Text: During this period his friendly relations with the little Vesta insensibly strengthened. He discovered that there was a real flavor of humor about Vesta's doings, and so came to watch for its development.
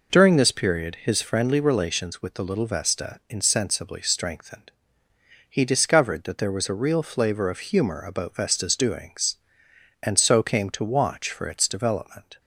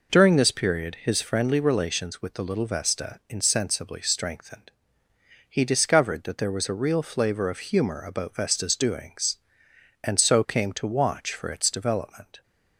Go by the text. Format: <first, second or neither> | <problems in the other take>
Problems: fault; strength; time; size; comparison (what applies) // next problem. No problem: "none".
neither | none